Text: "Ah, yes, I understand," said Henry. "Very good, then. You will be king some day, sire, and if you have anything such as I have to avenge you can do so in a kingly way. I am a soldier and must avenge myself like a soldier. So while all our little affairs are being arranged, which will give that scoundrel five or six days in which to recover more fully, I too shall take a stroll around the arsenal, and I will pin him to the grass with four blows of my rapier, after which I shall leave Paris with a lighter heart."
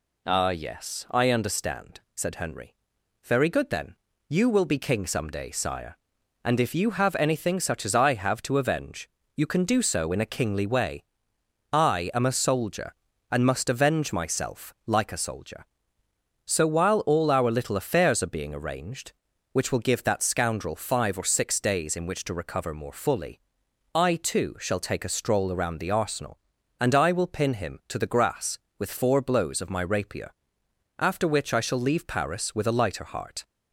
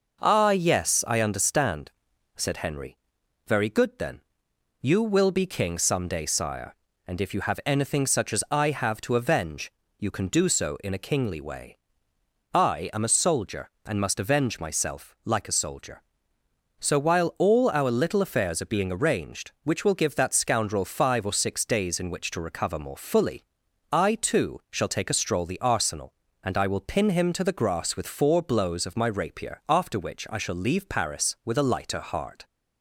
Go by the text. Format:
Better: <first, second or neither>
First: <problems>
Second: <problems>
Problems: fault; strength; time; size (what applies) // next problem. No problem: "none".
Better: first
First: pauses between "avenge" and "you"; slight; at 9.0 s; 0.26 s long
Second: pauses between "avenge" and "you"; slight; at 9.7 s; 0.30 s long // skips "around"; at 25.4 s